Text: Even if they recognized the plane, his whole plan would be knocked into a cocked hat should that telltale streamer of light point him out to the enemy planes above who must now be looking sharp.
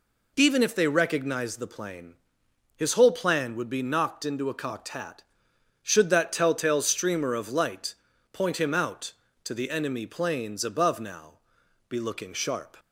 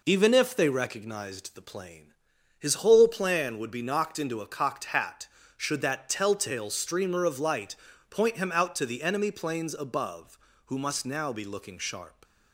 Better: second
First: pauses between "light" and "point"; at 7.9 s; 0.38 s long // skips "who must"; at 10.9 s // pauses between "now" and "be"; noticeable; at 11.3 s; 0.56 s long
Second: pauses between "light" and "point"; slight; at 7.7 s; 0.34 s long

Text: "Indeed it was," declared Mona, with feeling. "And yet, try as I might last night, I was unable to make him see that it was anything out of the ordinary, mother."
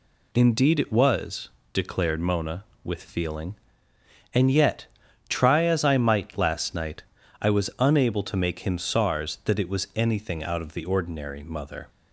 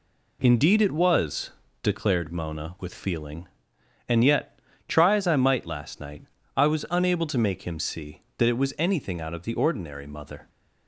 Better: second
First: says "sars" for "see"; at 8.7 s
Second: none

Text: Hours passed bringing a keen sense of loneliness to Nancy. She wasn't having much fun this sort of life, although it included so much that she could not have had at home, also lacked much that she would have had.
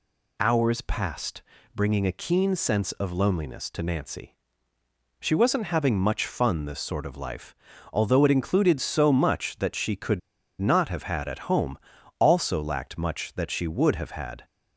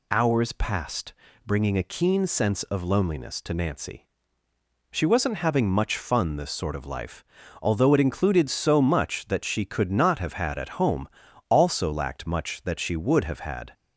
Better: second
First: pauses between "passed" and "bringing"; slight; at 1.4 s; 0.32 s long // pauses between "could" and "not"; at 10.1 s; 0.41 s long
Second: pauses between "passed" and "bringing"; slight; at 1.1 s; 0.32 s long

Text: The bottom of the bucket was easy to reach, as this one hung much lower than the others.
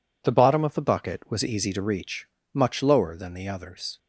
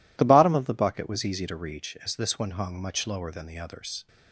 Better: second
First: skips "as this one hung"; at 2.4 s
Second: none

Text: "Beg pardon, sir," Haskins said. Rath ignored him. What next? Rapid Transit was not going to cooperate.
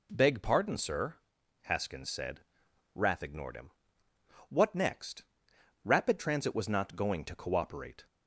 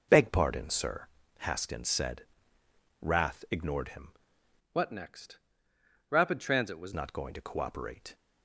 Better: first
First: none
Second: changes voice from "What" to "was"; from 4.7 to 6.9 s; 2.2 s long

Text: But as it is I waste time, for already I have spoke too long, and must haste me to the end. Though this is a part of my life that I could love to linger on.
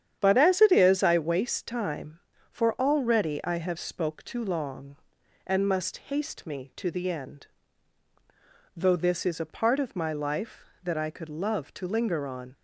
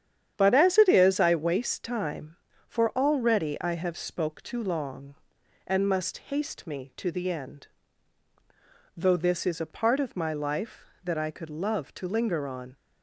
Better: neither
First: starts louder than the rest; strong; until 1.2 s; 9.5 dB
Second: starts louder than the rest; strong; until 1.3 s; 9.5 dB

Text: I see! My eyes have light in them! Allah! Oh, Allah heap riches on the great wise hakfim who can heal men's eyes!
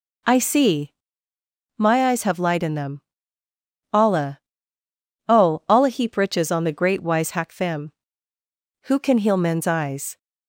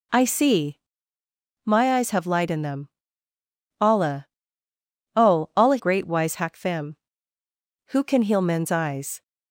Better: first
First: none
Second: skips "heap riches on the"; at 5.7 s

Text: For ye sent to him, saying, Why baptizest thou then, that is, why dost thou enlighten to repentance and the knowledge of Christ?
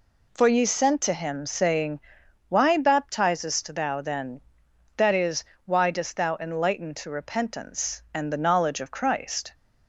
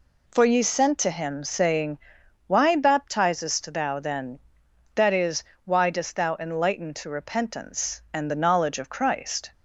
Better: neither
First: none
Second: none

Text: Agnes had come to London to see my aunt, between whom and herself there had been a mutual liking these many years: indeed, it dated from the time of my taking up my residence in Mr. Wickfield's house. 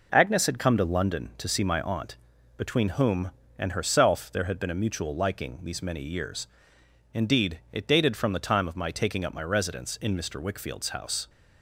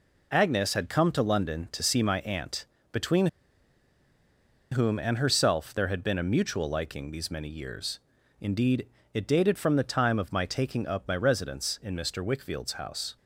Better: first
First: none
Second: pauses between "between" and "whom"; strong; at 3.2 s; 1.4 s long

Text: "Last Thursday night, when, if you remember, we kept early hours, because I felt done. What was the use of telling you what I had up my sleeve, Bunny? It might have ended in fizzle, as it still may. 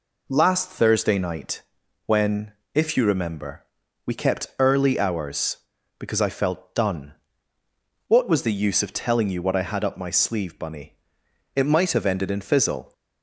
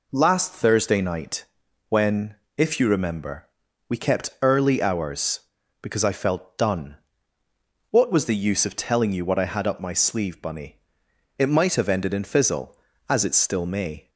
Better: second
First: stops before "as it still may"; at 12.9 s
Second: none

